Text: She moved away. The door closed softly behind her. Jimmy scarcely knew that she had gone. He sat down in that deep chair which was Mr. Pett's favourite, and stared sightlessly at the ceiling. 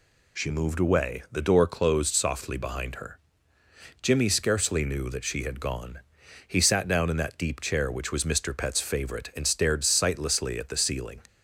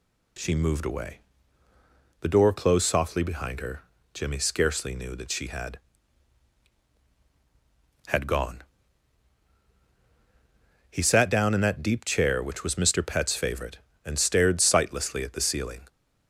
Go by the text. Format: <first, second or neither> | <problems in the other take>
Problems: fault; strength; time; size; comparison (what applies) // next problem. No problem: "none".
first | says "had" twice; at 8.0 s